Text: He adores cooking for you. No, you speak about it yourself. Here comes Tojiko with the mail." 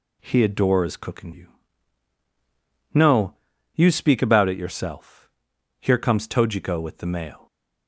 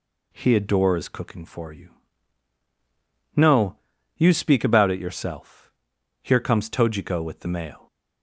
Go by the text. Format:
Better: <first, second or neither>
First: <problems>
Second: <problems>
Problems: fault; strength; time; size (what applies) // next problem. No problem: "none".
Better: second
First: skips "for"; at 1.3 s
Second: none